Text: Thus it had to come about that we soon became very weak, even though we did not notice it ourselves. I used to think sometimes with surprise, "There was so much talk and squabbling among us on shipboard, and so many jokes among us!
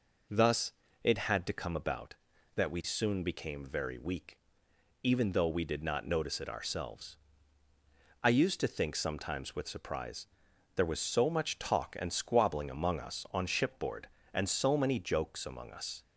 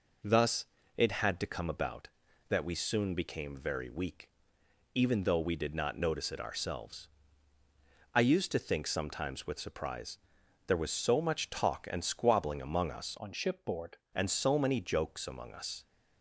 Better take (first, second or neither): first